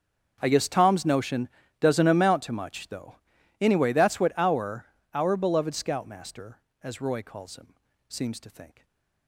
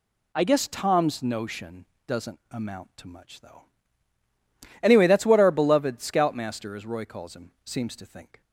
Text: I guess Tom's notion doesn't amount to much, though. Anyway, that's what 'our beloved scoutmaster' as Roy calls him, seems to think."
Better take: second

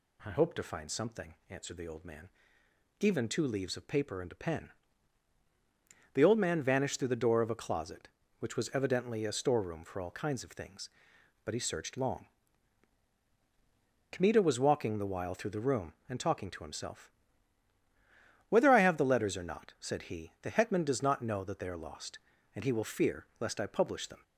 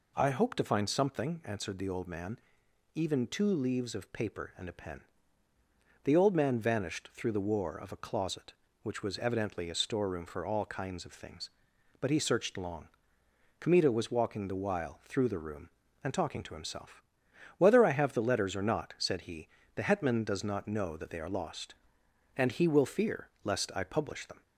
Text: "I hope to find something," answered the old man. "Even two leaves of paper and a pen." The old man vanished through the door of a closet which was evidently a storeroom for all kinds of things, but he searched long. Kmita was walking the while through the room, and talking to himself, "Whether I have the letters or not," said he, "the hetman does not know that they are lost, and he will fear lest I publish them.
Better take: first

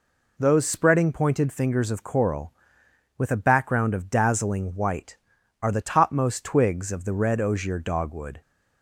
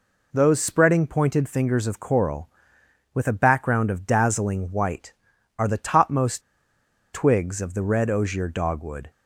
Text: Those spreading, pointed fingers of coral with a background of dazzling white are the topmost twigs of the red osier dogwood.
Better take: first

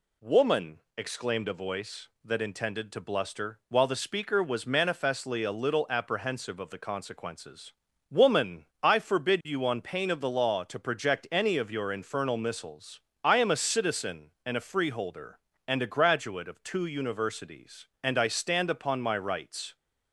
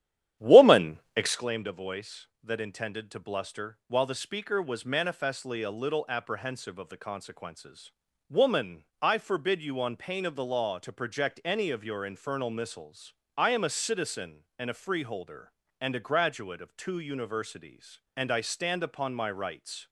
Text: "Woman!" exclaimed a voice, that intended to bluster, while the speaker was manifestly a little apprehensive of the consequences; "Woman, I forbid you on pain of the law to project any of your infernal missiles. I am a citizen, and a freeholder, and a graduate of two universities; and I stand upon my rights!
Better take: first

